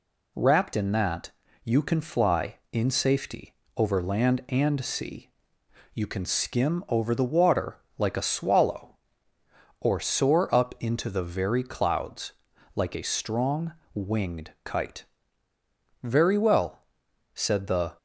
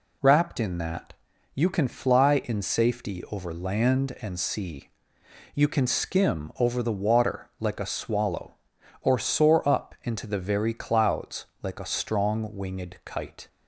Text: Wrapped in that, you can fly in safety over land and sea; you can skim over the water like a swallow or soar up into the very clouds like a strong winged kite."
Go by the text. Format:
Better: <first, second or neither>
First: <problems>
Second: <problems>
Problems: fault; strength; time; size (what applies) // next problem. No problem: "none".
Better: second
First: pauses between "safety" and "over"; slight; at 3.5 s; 0.22 s long // pauses between "water" and "like"; slight; at 7.7 s; 0.18 s long // pauses between "clouds" and "like"; at 12.3 s; 0.44 s long // pauses between "strong" and "winged"; slight; at 13.7 s; 0.20 s long // goes on to say "Very well said the"; strong; from 16.1 s on; 1.8 s long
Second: pauses between "clouds" and "like"; slight; at 11.4 s; 0.16 s long